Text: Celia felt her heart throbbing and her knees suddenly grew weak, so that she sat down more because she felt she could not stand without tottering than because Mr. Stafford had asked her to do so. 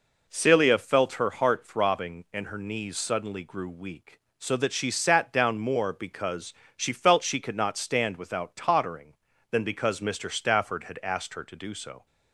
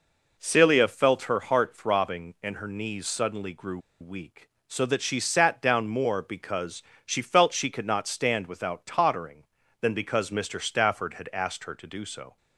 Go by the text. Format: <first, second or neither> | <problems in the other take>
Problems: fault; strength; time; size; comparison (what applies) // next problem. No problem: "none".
first | pauses between "grew" and "weak"; slight; at 3.7 s; 0.21 s long // pauses between "because" and "she"; slight; at 6.8 s; 0.22 s long; slight in the first